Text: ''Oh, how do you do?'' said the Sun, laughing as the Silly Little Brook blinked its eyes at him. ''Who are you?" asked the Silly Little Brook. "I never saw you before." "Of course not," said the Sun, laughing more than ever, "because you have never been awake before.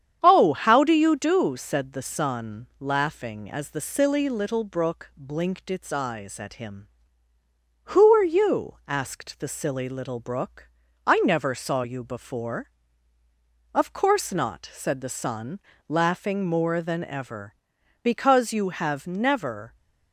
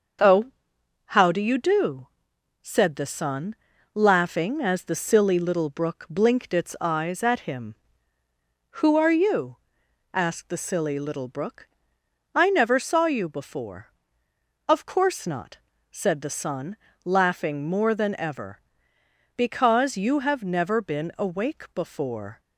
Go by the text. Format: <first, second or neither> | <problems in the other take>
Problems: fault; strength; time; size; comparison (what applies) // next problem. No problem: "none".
second | starts louder than the rest; strong; until 1.2 s; 9 dB; also in the second // stops before "been awake before"; at 19.7 s